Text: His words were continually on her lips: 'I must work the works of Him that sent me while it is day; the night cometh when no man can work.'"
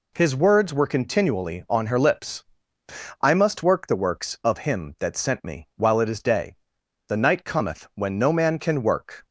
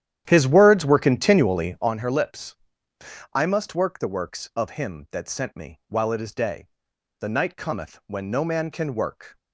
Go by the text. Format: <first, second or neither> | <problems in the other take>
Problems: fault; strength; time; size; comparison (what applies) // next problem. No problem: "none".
first | starts louder than the rest; strong; until 2.0 s; 11 dB